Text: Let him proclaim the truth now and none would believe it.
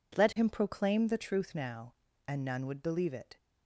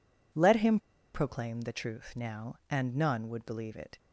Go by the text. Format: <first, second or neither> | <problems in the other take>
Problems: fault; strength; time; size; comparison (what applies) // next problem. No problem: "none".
first | pauses between "him" and "proclaim"; slight; at 0.7 s; 0.36 s long